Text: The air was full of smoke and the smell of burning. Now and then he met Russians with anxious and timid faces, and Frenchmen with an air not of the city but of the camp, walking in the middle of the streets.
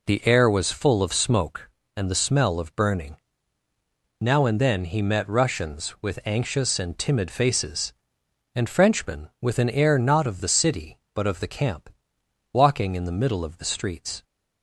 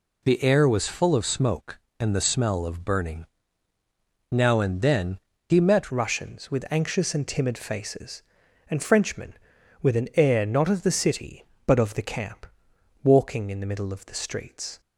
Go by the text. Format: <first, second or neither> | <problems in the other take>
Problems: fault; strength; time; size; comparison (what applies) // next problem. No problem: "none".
first | pauses between "then" and "he"; slight; at 5.1 s; 0.30 s long // changes voice at "Russians"; from 5.8 s on; 8.9 s long